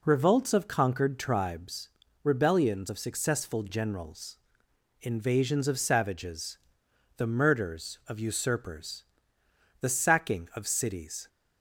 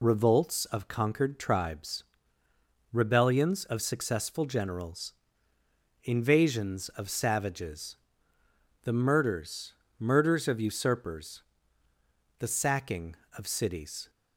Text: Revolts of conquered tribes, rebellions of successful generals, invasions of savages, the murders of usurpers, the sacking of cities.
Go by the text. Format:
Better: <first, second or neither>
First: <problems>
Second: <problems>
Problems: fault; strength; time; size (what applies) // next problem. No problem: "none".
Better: first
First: none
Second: says "murders" twice; at 9.9 s